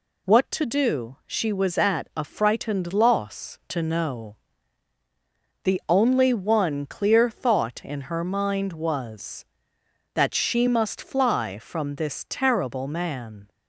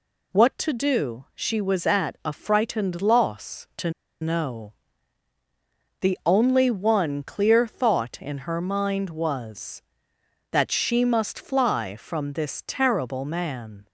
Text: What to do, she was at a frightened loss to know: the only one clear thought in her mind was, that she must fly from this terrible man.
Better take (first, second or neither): first